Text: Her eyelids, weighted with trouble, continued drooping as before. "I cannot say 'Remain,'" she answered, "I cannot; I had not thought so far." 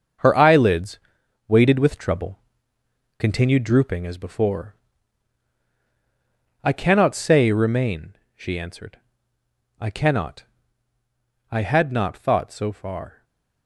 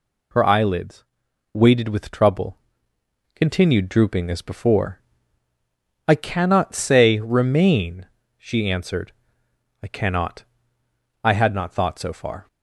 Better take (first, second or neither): second